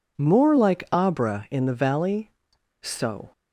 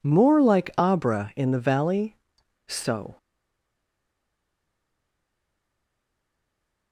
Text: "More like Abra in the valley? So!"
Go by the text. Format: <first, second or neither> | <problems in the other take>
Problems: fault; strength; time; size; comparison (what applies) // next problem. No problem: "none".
first | stays silent after the last word; strong; from 3.1 s on; 3.8 s long